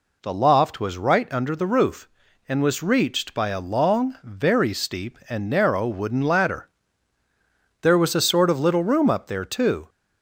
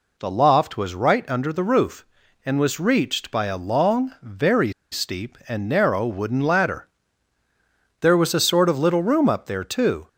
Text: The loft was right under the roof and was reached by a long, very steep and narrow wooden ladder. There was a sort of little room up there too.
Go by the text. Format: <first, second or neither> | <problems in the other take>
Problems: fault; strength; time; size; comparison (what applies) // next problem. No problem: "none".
first | pauses between "very" and "steep"; slight; at 4.7 s; 0.18 s long